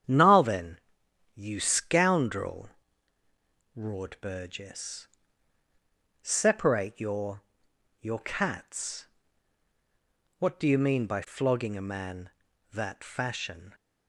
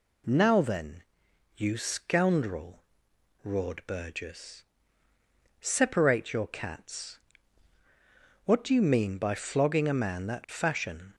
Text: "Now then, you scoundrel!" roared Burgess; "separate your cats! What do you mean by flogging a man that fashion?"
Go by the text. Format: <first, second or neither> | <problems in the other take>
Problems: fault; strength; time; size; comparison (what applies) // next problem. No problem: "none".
second | starts louder than the rest; strong; until 1.5 s; 9 dB // says "your" twice; at 8.0 s